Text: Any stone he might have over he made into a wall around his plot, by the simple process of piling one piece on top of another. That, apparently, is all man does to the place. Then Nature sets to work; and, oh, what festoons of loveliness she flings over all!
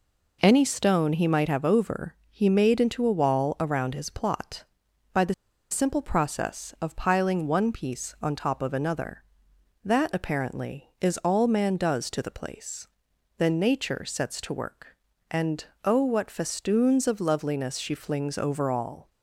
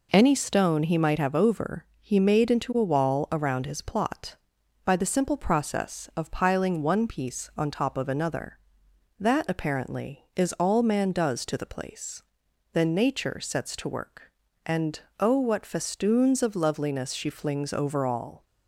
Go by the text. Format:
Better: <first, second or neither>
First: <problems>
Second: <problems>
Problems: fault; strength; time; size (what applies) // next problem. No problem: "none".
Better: second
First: pauses between "the" and "simple"; at 5.3 s; 0.37 s long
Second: none